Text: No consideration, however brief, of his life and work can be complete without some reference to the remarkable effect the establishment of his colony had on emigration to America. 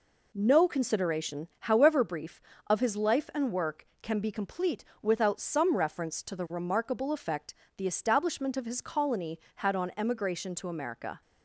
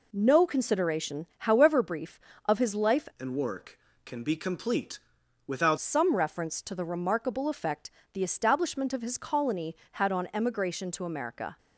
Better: first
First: pauses between "complete" and "without"; slight; at 4.8 s; 0.18 s long // pauses between "effect" and "the"; slight; at 7.5 s; 0.24 s long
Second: changes voice from "and" to "without"; from 3.1 to 5.7 s; 2.6 s long // pauses between "complete" and "without"; noticeable; at 4.9 s; 0.48 s long // pauses between "effect" and "the"; slight; at 7.8 s; 0.24 s long

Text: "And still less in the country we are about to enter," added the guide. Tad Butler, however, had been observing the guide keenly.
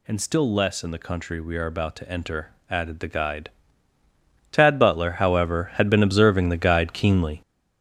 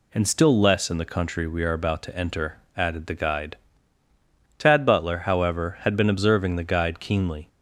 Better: second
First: gets louder; strong; throughout; 8 dB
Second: none

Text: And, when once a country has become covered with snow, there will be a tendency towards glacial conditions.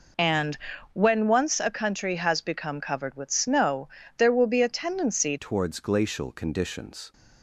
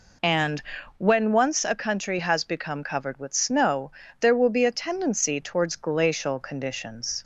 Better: second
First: changes voice at "towards"; from 5.3 s on; 1.8 s long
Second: none

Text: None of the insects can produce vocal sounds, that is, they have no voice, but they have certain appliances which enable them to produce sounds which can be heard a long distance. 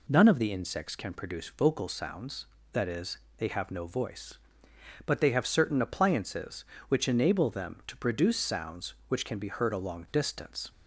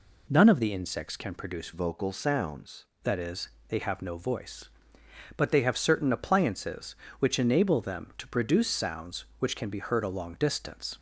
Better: first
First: none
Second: changes voice from "vocal" to "sounds"; from 1.7 to 2.8 s; 1.1 s long

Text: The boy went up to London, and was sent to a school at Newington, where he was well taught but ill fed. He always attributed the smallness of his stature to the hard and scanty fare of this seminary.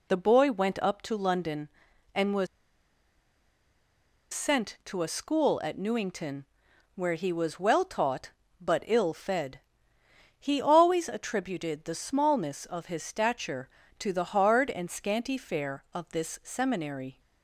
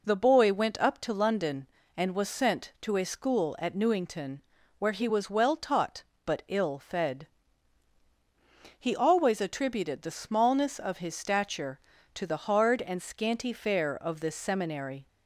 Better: second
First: pauses between "was" and "sent"; strong; at 2.4 s; 1.8 s long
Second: none

